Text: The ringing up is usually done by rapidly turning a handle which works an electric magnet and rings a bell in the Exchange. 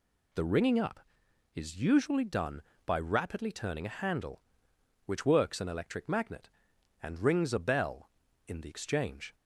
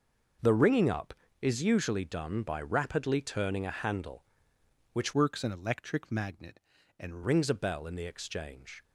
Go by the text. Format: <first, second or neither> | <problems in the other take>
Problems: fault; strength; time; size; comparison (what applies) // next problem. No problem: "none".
first | starts louder than the rest; noticeable; until 1.7 s; 6 dB // changes voice from "works" to "and"; from 5.1 to 7.2 s; 2.1 s long